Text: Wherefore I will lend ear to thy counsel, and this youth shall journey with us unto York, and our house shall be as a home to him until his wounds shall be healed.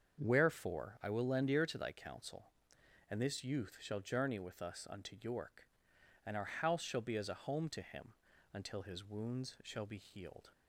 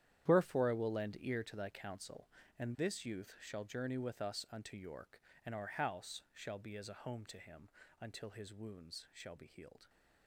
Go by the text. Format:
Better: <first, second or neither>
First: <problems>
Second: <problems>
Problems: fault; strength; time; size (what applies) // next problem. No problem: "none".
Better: first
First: starts louder than the rest; until 1.2 s; 7 dB // pauses between "him" and "until"; at 8.1 s; 0.40 s long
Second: gets quieter; strong; throughout; 14 dB // starts louder than the rest; strong; until 1.3 s; 10.5 dB // pauses between "him" and "until"; slight; at 7.6 s; 0.30 s long